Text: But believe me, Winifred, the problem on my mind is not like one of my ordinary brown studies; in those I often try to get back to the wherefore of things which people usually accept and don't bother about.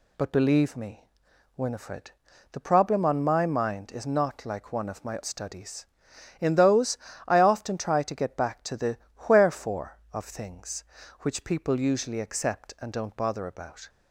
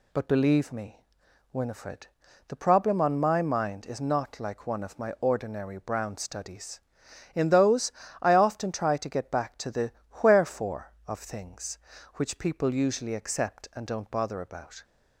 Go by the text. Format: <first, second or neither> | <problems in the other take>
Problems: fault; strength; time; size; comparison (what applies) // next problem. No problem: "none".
second | skips "ordinary brown"; at 5.2 s // pauses between "those" and "I"; slight; at 6.9 s; 0.30 s long; slight in the second // pauses between "the" and "wherefore"; slight; at 8.9 s; 0.32 s long; slight in the second